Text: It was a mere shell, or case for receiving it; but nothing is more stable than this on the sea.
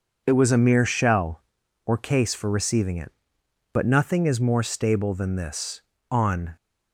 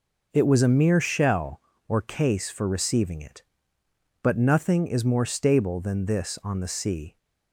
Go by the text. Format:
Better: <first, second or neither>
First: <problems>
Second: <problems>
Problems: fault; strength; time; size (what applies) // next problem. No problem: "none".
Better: second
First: stops before "the sea"; at 6.5 s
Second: none